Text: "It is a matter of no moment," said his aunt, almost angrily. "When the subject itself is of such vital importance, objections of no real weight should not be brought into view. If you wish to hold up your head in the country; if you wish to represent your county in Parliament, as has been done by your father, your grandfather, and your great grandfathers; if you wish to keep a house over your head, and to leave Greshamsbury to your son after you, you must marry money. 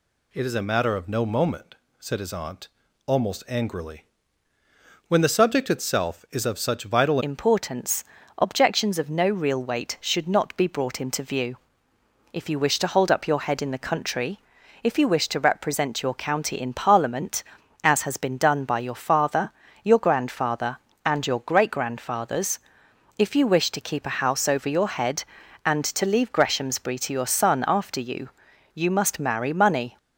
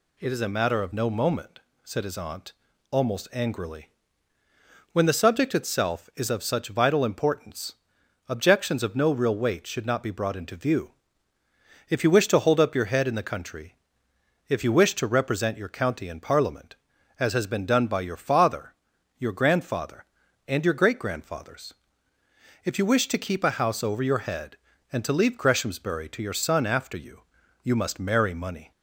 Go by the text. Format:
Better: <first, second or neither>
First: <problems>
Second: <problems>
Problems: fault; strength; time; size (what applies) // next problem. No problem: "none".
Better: second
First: changes voice at "importance"; from 7.2 s on; 22.7 s long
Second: none